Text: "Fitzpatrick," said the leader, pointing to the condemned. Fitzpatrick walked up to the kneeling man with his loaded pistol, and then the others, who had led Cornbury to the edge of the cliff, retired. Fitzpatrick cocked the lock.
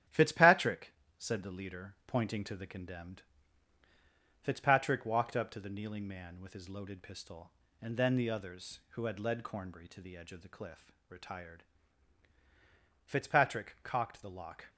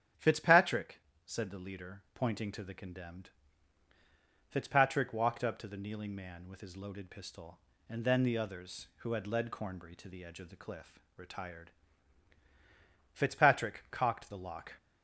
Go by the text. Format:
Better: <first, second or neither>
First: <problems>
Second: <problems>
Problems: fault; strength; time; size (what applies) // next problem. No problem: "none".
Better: second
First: gets quieter; noticeable; throughout; 5 dB // starts louder than the rest; strong; until 1.3 s; 10 dB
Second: starts louder than the rest; strong; until 1.4 s; 8.5 dB